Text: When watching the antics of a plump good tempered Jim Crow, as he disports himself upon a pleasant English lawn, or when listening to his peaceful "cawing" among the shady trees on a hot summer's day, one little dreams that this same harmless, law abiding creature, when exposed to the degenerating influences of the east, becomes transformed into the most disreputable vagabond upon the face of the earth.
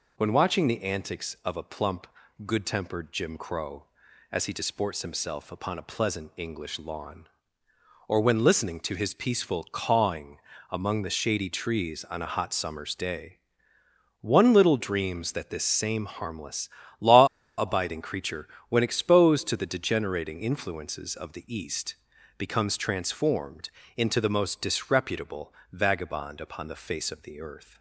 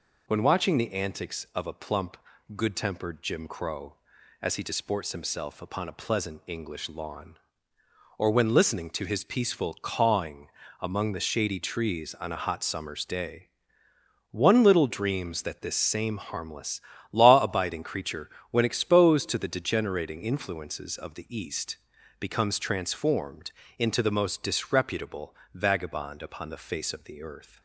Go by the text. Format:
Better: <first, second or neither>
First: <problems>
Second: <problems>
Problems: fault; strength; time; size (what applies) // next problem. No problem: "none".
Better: second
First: pauses between "plump" and "good"; at 2.0 s; 0.40 s long // pauses between "cawing" and "among"; slight; at 10.3 s; 0.32 s long // pauses between "law" and "abiding"; slight; at 17.2 s; 0.32 s long // pauses between "transformed" and "into"; slight; at 23.6 s; 0.28 s long // pauses between "disreputable" and "vagabond"; slight; at 25.5 s; 0.20 s long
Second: pauses between "plump" and "good"; at 2.1 s; 0.40 s long // pauses between "cawing" and "among"; slight; at 10.4 s; 0.32 s long // pauses between "transformed" and "into"; slight; at 23.4 s; 0.28 s long // pauses between "disreputable" and "vagabond"; slight; at 25.3 s; 0.20 s long